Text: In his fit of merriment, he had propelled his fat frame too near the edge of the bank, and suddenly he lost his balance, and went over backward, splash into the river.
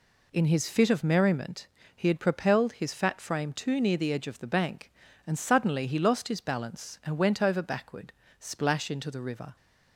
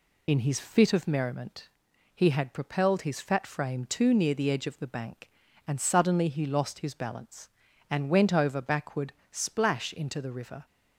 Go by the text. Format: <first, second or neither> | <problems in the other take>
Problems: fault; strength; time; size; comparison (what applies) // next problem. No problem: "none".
first | loses the start of "In"; at 0.2 s; 45 ms